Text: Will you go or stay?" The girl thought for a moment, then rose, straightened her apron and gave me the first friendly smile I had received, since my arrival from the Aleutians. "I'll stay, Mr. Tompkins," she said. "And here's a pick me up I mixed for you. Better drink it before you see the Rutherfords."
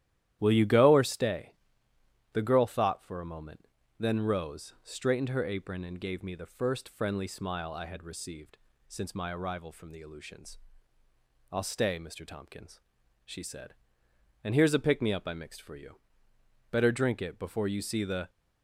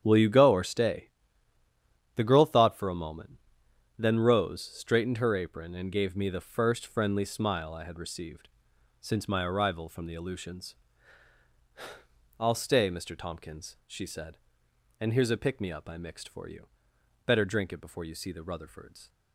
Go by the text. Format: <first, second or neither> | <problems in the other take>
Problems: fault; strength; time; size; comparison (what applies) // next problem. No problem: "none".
second | starts louder than the rest; strong; until 1.4 s; 12 dB; strong in the second // stops before "Rutherfords"; at 18.2 s